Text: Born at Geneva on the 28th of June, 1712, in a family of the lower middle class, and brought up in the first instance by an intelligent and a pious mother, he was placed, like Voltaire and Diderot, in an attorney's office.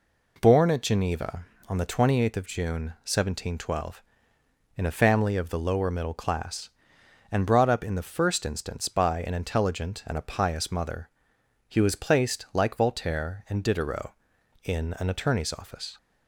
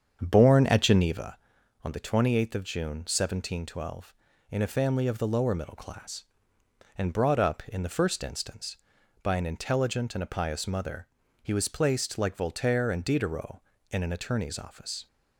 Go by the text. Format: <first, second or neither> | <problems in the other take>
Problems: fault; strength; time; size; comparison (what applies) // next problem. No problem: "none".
first | starts louder than the rest; strong; until 1.3 s; 7.5 dB